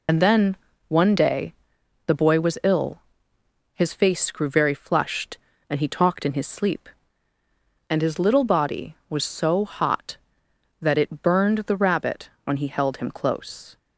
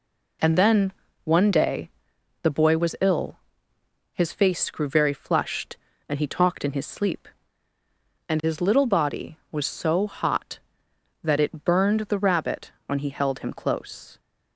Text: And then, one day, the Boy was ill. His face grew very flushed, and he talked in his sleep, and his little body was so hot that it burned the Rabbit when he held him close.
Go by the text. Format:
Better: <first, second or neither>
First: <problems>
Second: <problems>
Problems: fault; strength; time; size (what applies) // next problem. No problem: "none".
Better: second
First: loses the start of "And"; at 0.0 s; 45 ms // pauses between "Rabbit" and "when"; slight; at 12.2 s; 0.16 s long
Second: pauses between "Rabbit" and "when"; slight; at 12.7 s; 0.16 s long